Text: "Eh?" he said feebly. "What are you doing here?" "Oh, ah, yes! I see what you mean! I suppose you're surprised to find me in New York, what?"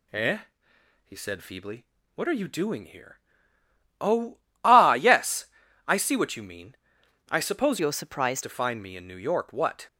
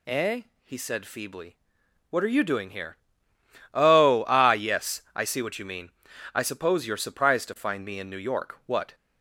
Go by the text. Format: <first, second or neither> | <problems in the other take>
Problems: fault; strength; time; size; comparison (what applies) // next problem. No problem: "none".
second | changes voice from "you're" to "surprised"; from 7.7 to 8.4 s; 0.7 s long